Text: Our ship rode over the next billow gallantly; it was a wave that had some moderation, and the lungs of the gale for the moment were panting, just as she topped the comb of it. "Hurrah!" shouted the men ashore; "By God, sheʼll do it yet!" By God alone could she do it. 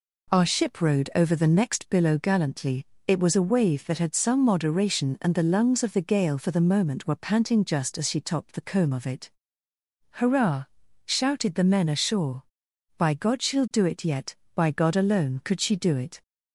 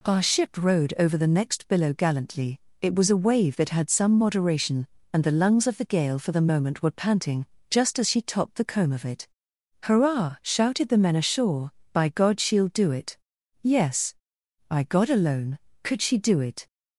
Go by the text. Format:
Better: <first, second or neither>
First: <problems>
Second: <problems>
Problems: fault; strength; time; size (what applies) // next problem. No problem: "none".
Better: first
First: none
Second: says "yes" for "yet"; at 13.6 s